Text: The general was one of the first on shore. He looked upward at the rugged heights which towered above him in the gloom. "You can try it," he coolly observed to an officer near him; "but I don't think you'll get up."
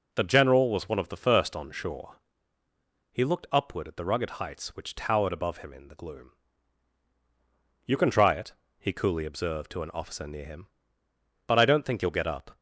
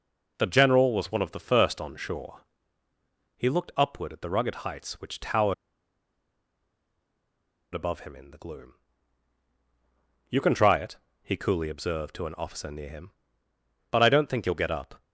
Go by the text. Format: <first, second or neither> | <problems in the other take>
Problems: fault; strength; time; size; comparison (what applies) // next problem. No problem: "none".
first | pauses between "towered" and "above"; strong; at 5.5 s; 2.1 s long